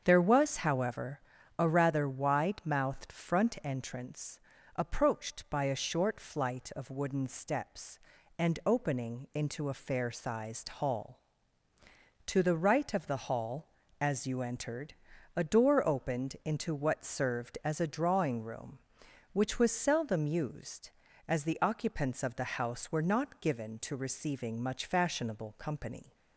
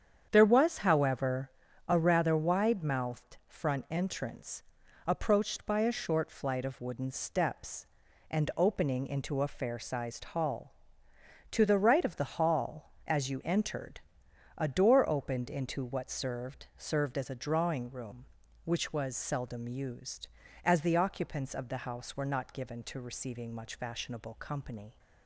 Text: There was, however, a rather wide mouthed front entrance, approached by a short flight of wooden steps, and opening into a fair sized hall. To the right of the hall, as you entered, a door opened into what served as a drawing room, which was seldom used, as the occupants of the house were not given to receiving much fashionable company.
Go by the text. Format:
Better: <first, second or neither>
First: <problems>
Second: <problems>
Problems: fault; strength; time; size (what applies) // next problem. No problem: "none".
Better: first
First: starts louder than the rest; strong; until 1.0 s; 7.5 dB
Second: starts louder than the rest; strong; until 1.3 s; 8 dB // says "served" twice; at 16.7 s